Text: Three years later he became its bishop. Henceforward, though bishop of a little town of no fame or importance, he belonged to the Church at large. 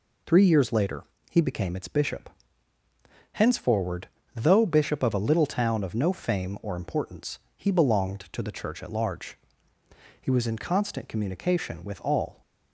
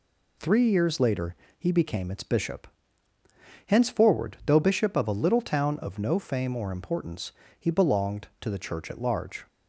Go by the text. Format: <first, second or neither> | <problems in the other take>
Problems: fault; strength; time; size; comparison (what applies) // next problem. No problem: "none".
second | pauses between "later" and "he"; slight; at 1.0 s; 0.26 s long; slight in the second // goes on to say "He was in constant communication with all"; strong; from 10.2 s on; 2.2 s long